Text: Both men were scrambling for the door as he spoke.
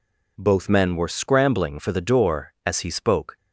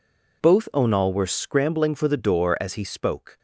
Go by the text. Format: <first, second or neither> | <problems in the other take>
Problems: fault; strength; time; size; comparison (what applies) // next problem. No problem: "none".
first | says "onal" for "men"; at 0.7 s